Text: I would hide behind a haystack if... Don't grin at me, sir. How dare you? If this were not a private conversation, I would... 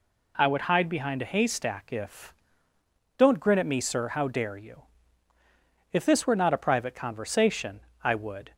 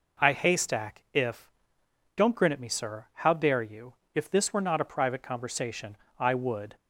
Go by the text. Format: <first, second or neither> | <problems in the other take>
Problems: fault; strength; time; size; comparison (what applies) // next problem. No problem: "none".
first | skips "would hide behind a"; at 0.3 s